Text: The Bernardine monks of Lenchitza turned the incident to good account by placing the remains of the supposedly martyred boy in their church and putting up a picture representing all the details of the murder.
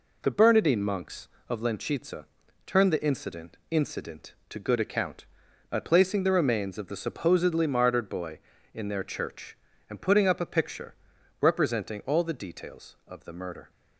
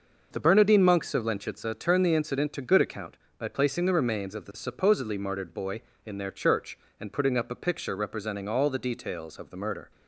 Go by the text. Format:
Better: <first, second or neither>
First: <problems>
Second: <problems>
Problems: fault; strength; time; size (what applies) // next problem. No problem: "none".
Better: second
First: pauses between "Lenchitza" and "turned"; at 2.2 s; 0.42 s long // says "incident" twice; at 3.7 s // pauses between "picture" and "representing"; noticeable; at 10.9 s; 0.46 s long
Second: none